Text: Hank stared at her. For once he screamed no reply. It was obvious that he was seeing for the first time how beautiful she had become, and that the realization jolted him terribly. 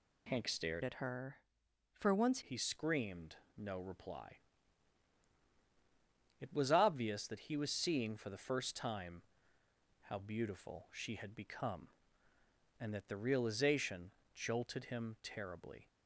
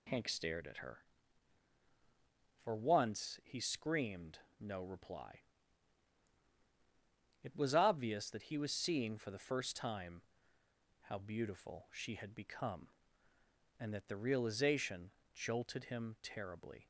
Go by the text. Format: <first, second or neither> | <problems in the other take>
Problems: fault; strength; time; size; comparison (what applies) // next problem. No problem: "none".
second | changes voice from "at" to "once"; from 0.8 to 2.4 s; 1.6 s long // pauses between "screamed" and "no"; slight; at 3.3 s; 0.22 s long; slight in the second // pauses between "time" and "how"; noticeable; at 9.2 s; 0.86 s long; noticeable in the second // pauses between "realization" and "jolted"; slight; at 14.1 s; 0.24 s long; slight in the second